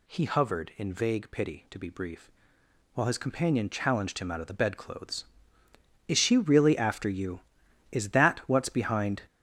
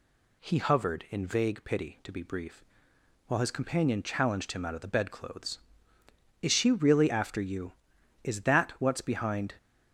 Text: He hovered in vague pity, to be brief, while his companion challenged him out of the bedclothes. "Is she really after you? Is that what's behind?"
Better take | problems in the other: second | gets louder; strong; throughout; 8 dB

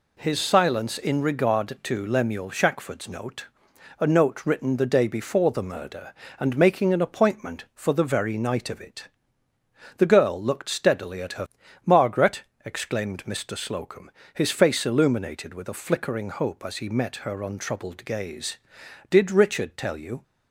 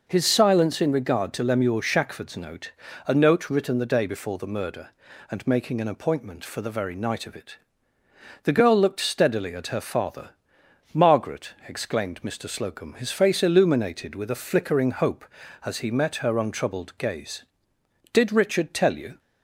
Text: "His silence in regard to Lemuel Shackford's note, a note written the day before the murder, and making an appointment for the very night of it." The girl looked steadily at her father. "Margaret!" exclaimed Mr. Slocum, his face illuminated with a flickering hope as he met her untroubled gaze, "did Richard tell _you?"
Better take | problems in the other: second | skips "father"; at 11.6 s

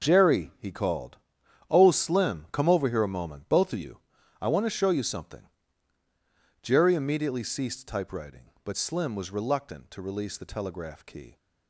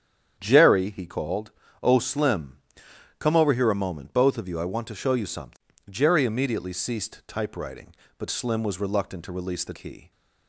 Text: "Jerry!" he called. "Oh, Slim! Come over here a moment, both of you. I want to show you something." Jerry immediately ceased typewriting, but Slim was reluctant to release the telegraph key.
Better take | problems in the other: first | starts louder than the rest; strong; until 1.4 s; 8.5 dB // skips "telegraph"; at 9.7 s

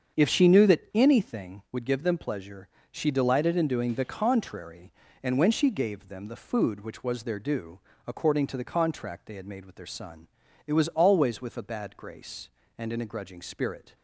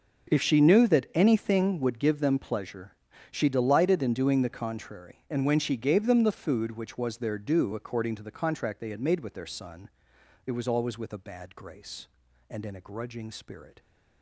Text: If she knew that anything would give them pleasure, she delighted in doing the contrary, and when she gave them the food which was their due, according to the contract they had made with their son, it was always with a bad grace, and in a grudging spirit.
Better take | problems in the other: neither | starts louder than the rest; the same in both

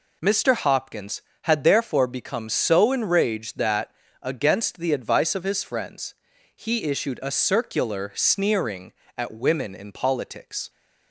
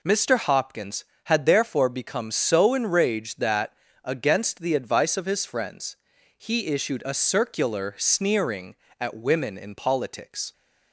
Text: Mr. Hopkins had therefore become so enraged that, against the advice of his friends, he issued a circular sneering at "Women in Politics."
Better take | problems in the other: neither | none

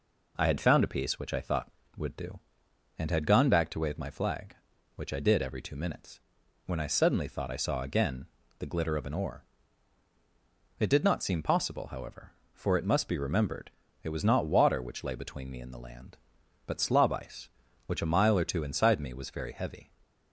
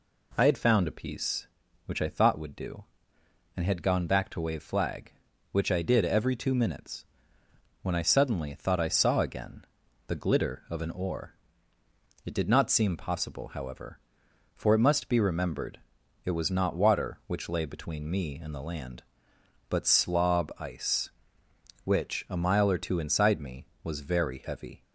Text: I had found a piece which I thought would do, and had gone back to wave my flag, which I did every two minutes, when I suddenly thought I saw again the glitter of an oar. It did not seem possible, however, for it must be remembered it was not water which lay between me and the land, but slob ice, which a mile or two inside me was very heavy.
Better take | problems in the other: first | skips "my"; at 4.6 s // pauses between "again" and "the"; at 9.6 s; 0.40 s long; slight in the first // pauses between "remembered" and "it"; at 15.8 s; 0.44 s long; slight in the first

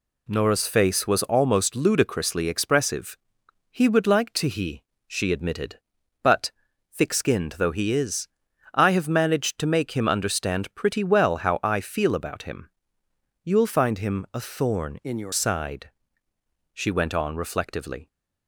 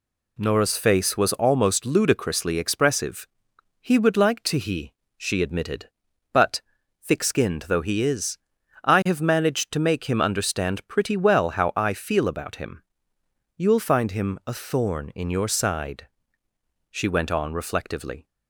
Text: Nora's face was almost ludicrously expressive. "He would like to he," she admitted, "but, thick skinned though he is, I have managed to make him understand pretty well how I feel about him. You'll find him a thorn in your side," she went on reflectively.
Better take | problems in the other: second | changes voice from "in" to "your"; from 15.0 to 15.3 s; 0.3 s long

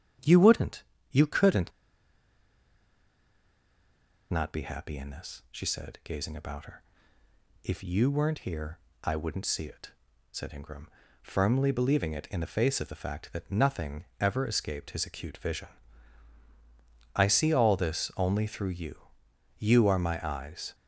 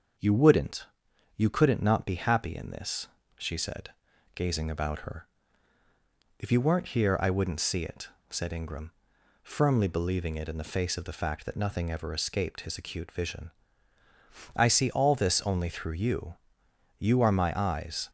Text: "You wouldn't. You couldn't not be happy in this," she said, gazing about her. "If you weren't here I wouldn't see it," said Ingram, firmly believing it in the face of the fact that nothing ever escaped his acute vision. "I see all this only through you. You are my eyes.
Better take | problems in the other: second | starts louder than the rest; strong; until 1.5 s; 9 dB; also in the second // pauses between "couldn't" and "not"; strong; at 1.7 s; 2.5 s long // pauses between "here" and "I"; slight; at 8.7 s; 0.24 s long // pauses between "nothing" and "ever"; slight; at 14.0 s; 0.16 s long

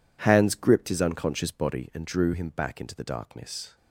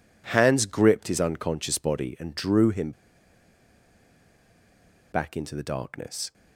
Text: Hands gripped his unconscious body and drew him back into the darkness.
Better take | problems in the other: first | pauses between "him" and "back"; strong; at 2.9 s; 2.2 s long

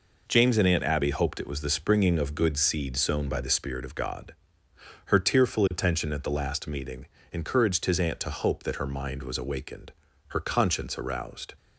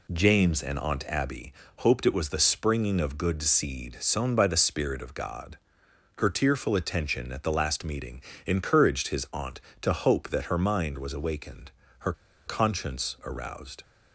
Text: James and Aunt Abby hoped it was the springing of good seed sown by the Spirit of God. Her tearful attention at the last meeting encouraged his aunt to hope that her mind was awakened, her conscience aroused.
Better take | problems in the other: first | pauses between "Abby" and "hoped"; slight; at 1.5 s; 0.26 s long // pauses between "meeting" and "encouraged"; slight; at 8.2 s; 0.24 s long; slight in the first // pauses between "her" and "conscience"; slight; at 12.1 s; 0.34 s long

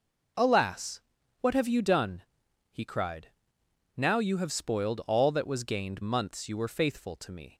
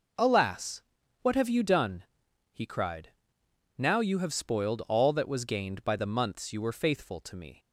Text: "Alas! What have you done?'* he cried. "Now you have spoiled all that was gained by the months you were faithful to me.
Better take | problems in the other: second | skips "by the"; at 6.0 s

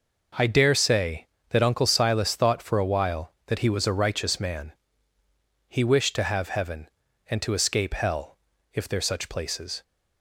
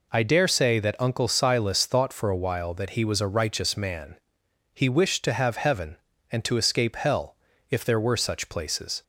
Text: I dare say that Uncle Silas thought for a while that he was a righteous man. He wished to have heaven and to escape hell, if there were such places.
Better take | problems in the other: second | skips "were"; at 9.0 s

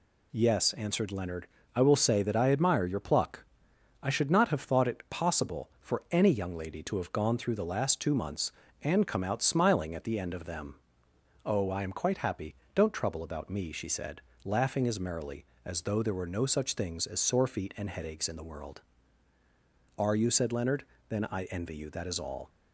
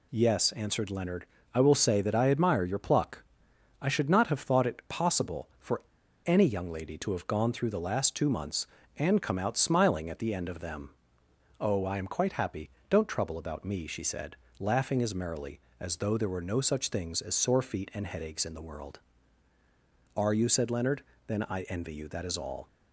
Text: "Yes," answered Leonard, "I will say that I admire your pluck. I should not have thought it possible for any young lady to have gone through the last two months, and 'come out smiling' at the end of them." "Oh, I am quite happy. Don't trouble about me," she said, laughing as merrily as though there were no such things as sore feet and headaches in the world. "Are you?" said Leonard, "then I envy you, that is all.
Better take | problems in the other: first | pauses between "for" and "any"; at 5.8 s; 0.44 s long

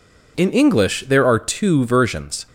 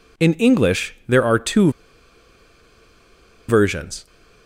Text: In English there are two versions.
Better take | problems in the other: first | pauses between "two" and "versions"; strong; at 1.6 s; 1.7 s long

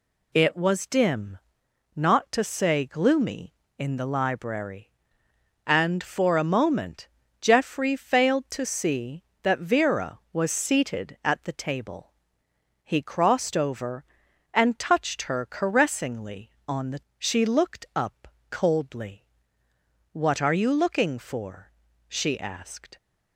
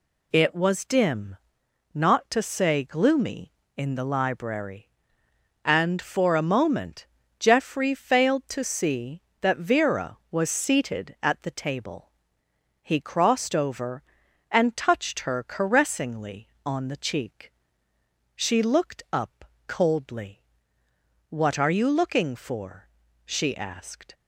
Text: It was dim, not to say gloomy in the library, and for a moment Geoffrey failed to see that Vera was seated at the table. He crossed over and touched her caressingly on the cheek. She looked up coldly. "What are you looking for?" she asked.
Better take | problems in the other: second | pauses between "moment" and "Geoffrey"; slight; at 7.0 s; 0.36 s long; slight in the second // skips "cheek"; at 17.1 s // pauses between "up" and "coldly"; slight; at 18.2 s; 0.20 s long; slight in the second

